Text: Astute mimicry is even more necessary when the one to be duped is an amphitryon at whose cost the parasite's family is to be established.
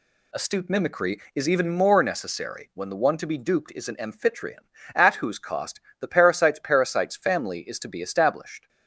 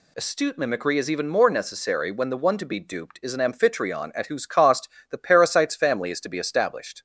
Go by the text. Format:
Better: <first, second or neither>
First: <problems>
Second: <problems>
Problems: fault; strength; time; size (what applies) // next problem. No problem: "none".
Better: second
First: pauses between "cost" and "the"; slight; at 5.8 s; 0.18 s long // says "parasite's" twice; at 6.6 s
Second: pauses between "cost" and "the"; slight; at 4.8 s; 0.20 s long